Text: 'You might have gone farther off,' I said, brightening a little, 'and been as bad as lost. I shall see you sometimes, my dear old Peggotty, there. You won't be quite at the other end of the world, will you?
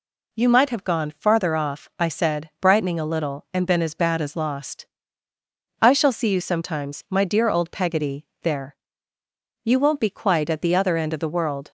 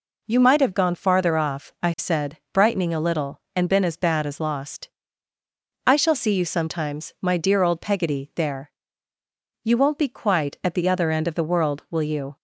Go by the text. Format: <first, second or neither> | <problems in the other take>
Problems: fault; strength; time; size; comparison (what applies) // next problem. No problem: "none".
second | stops before "will you"; at 11.6 s